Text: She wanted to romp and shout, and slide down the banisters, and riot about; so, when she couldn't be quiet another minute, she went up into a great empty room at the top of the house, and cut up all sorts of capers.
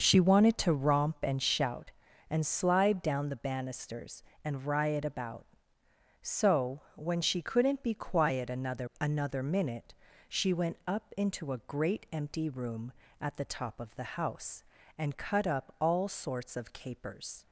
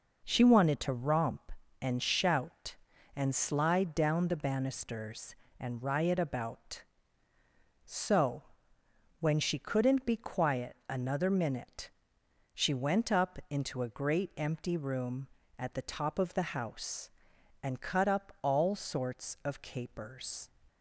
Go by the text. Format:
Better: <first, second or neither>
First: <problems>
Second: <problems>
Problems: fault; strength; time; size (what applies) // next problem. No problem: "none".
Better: second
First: says "another" twice; at 8.9 s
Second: none